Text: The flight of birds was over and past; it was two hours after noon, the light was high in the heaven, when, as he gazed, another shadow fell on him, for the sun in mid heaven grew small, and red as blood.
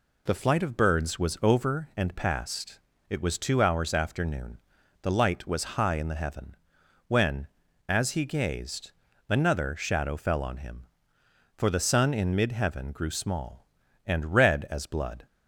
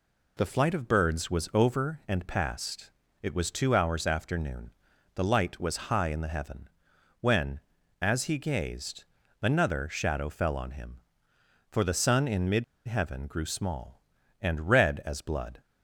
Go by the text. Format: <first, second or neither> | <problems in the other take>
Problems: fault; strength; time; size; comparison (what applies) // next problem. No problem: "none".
first | pauses between "mid" and "heaven"; slight; at 12.6 s; 0.22 s long